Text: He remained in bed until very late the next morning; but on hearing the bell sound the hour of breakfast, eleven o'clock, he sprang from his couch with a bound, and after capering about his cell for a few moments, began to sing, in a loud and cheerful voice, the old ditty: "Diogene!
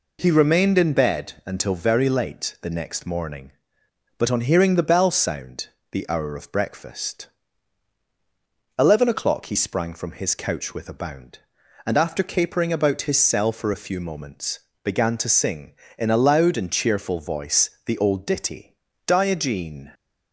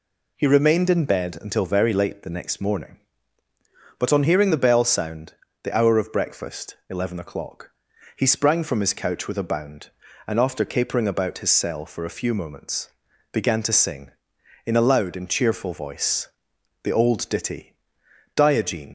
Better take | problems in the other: first | pauses between "sound" and "the"; slight; at 5.3 s; 0.28 s long; slight in the first // leaves "Diogene" unfinished; at 18.8 s; 85 ms

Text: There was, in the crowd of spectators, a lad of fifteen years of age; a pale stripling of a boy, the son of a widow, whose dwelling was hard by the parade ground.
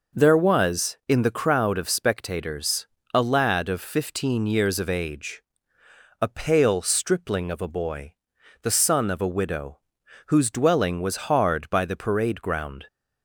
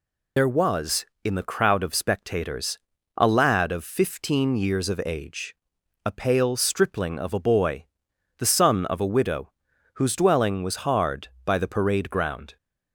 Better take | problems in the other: first | loses the start of "There"; at 0.3 s; 120 ms

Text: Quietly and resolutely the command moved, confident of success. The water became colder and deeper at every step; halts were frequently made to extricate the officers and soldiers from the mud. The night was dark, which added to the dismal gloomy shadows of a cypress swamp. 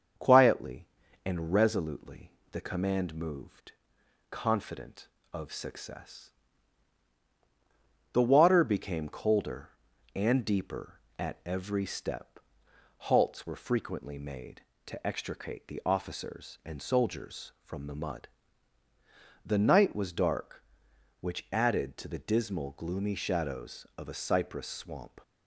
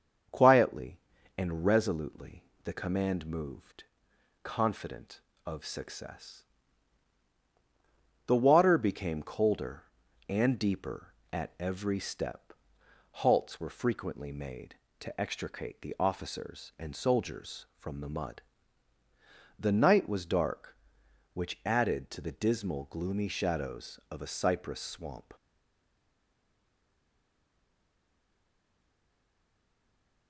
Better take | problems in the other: first | starts louder than the rest; until 1.6 s; 6.5 dB; also in the first // pauses between "resolutely" and "the"; slight; at 2.4 s; 0.20 s long; slight in the first // stays silent after the last word; strong; from 25.3 s on; 4.9 s long

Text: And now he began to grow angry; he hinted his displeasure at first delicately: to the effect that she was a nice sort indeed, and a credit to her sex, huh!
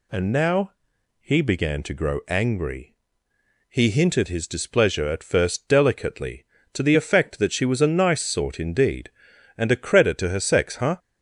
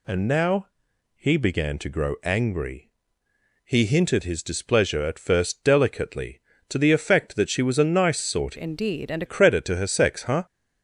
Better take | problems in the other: first | pauses between "now" and "he"; noticeable; at 0.6 s; 0.50 s long; noticeable in the first // changes voice from "indeed" to "a"; from 8.5 to 9.2 s; 0.7 s long

